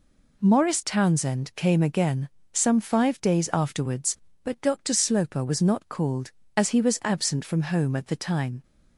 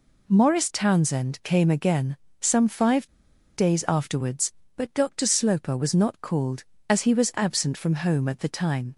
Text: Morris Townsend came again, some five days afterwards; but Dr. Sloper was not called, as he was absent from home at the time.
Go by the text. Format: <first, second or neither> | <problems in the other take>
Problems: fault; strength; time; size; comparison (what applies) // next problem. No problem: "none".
first | pauses between "five" and "days"; noticeable; at 3.0 s; 0.48 s long